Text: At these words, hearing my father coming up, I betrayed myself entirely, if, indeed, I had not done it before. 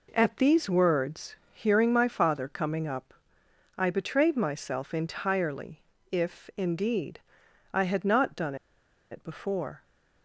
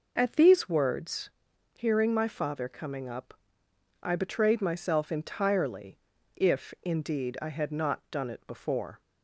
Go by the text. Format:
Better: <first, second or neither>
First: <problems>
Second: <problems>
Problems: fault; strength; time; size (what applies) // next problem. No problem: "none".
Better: second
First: pauses between "done" and "it"; noticeable; at 8.5 s; 0.55 s long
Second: none